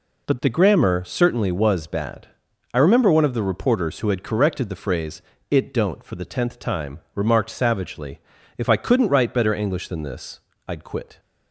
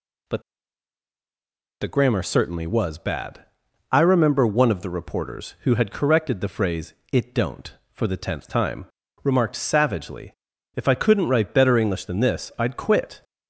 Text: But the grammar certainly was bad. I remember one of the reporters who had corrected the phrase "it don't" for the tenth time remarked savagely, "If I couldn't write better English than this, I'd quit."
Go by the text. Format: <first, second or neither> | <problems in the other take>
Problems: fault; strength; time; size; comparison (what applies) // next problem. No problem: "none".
first | pauses between "But" and "the"; strong; at 0.4 s; 1.3 s long // pauses between "phrase" and "it"; slight; at 6.9 s; 0.18 s long; slight in the first // pauses between "time" and "remarked"; at 8.8 s; 0.38 s long; slight in the first